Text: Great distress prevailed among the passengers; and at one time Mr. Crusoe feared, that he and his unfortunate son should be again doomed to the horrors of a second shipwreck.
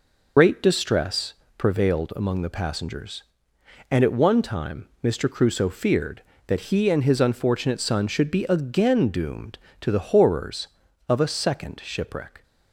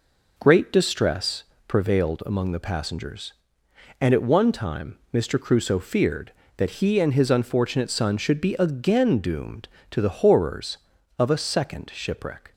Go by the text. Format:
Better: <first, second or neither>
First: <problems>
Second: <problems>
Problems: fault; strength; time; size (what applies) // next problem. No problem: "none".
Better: second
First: loses the start of "Great"; at 0.3 s; 80 ms // pauses between "distress" and "prevailed"; slight; at 1.3 s; 0.24 s long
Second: pauses between "distress" and "prevailed"; slight; at 1.4 s; 0.24 s long